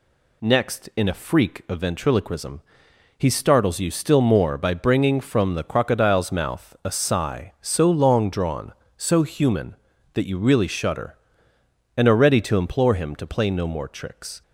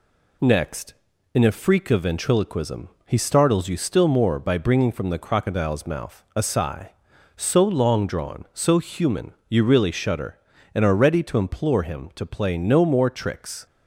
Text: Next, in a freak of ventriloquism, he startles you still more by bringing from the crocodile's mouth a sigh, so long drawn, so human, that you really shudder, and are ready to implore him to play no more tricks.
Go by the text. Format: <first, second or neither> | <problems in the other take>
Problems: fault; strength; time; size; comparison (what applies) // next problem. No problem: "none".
first | skips "that"; at 9.4 s